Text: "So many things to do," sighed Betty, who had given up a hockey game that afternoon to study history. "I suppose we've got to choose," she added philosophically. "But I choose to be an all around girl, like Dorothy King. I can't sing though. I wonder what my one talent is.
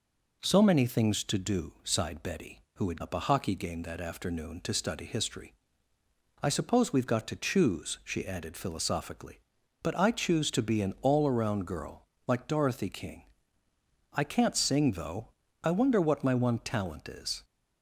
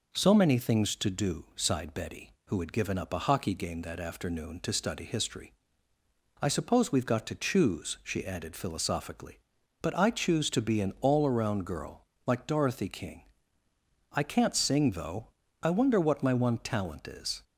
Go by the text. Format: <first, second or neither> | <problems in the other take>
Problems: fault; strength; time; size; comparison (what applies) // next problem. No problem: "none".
second | skips "given"; at 3.0 s